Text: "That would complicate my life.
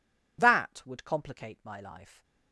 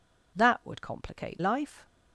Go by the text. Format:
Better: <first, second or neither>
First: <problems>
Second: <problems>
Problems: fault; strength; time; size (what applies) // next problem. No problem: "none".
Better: first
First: none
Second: skips "my"; at 1.3 s